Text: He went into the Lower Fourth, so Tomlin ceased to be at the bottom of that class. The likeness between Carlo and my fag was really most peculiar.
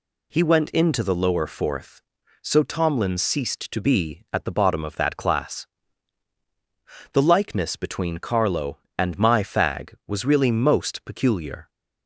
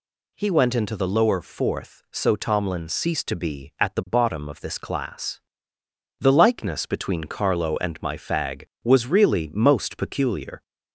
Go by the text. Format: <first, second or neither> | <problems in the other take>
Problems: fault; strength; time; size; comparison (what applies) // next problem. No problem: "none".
first | says "this" for "that"; at 4.6 s